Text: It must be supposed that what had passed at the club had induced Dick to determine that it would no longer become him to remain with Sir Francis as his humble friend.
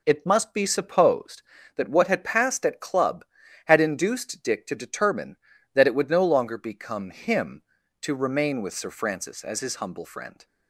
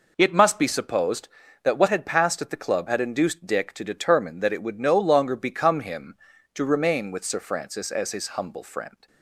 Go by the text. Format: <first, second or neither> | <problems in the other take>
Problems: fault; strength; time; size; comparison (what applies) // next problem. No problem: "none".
second | skips "the"; at 2.8 s